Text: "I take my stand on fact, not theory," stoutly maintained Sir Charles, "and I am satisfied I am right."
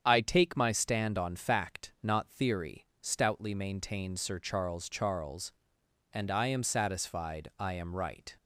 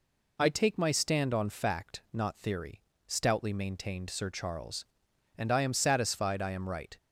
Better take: second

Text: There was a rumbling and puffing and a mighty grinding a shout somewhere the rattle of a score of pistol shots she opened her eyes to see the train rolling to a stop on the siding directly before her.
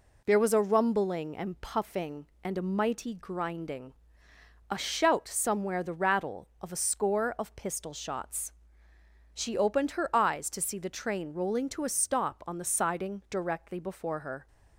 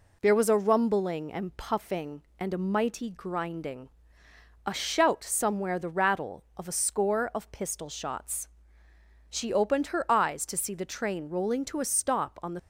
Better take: first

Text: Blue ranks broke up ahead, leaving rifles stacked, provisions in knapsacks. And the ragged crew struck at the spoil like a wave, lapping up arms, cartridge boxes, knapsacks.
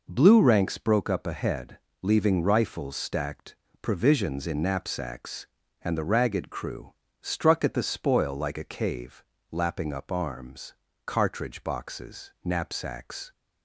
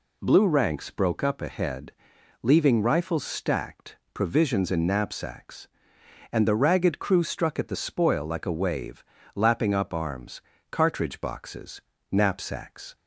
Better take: second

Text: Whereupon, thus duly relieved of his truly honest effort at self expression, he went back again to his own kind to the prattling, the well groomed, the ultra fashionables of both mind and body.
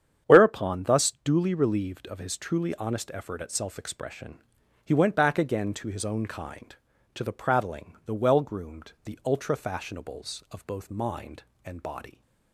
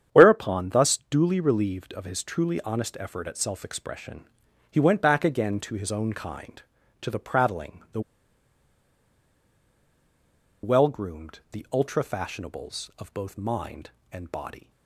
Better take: first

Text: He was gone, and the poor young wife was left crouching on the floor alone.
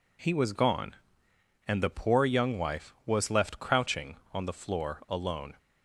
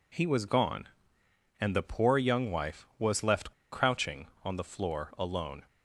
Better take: first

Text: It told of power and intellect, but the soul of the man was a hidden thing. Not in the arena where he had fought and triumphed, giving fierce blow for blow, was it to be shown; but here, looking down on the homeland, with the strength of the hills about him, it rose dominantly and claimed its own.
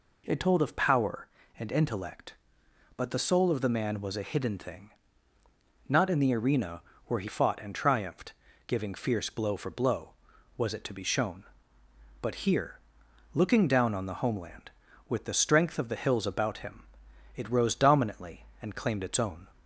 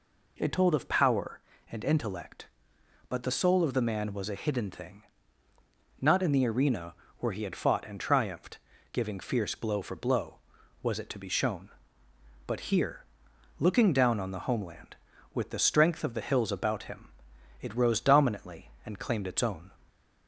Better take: second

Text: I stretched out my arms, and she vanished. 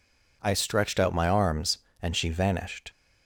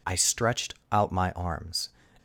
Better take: first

